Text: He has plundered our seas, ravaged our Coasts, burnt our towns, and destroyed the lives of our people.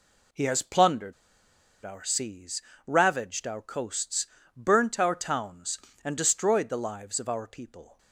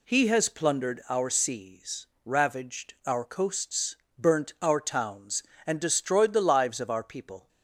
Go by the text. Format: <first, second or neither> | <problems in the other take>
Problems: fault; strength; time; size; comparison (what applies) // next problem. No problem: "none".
second | pauses between "plundered" and "our"; noticeable; at 1.1 s; 0.72 s long